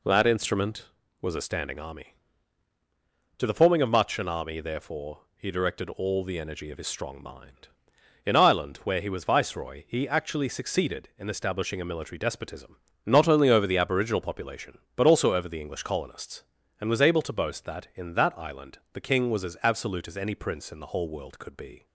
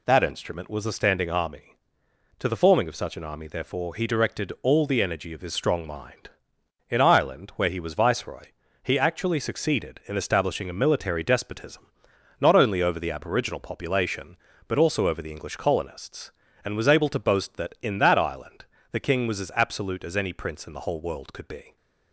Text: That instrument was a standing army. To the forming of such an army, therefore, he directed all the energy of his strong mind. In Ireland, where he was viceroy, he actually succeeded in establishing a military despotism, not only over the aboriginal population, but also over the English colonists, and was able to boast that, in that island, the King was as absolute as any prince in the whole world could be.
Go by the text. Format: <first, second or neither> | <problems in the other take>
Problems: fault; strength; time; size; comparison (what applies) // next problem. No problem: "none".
second | says "much" for "such"; at 3.8 s